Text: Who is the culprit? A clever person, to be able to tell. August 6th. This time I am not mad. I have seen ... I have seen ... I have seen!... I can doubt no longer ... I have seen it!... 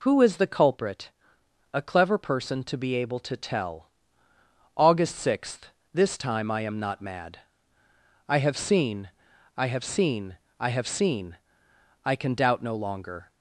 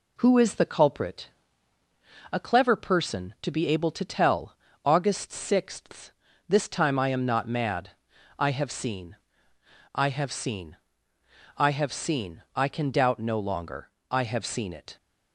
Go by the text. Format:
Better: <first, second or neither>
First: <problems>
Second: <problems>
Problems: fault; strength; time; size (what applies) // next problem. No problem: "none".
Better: second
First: stops before "I have seen it"; at 13.2 s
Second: none